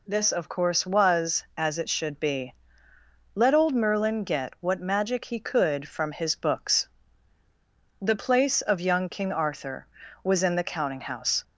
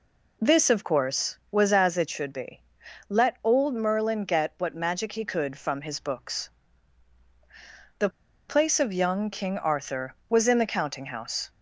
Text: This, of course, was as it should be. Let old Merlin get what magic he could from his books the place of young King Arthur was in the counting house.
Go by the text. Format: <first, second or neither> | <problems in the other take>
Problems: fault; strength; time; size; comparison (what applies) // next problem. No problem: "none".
first | pauses between "books" and "the"; strong; at 6.4 s; 1.5 s long; also in the first // pauses between "the" and "place"; at 8.0 s; 0.40 s long